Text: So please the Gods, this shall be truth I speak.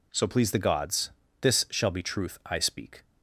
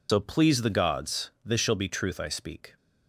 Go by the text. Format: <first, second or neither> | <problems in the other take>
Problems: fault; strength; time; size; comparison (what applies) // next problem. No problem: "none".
first | loses the start of "So"; at 0.0 s; 100 ms